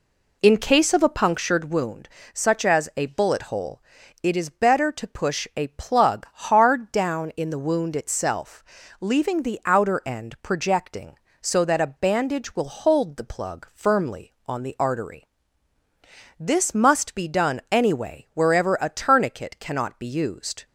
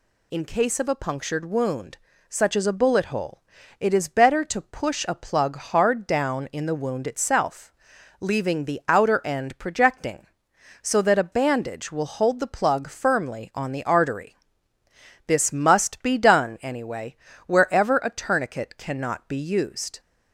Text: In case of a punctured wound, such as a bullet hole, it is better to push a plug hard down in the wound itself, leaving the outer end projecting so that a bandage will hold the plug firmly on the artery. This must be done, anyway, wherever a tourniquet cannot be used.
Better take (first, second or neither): second